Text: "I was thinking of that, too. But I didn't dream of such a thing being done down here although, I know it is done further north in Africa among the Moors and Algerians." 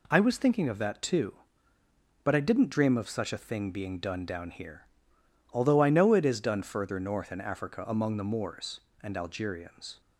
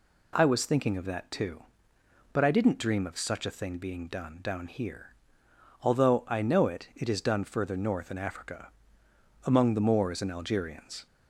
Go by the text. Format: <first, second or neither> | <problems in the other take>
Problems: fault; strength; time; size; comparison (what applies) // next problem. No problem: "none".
first | pauses between "here" and "although"; noticeable; at 5.1 s; 0.72 s long; noticeable in the first // says "it" twice; at 6.9 s // pauses between "Africa" and "among"; noticeable; at 8.7 s; 0.74 s long